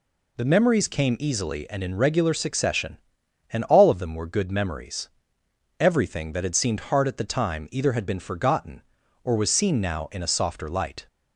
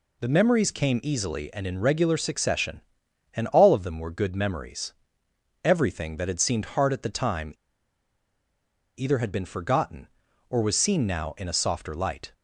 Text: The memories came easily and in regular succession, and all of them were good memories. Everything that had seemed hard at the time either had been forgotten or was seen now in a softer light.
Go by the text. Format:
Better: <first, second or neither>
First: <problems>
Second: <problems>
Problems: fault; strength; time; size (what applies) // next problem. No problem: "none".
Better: first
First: none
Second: pauses between "time" and "either"; strong; at 7.5 s; 1.4 s long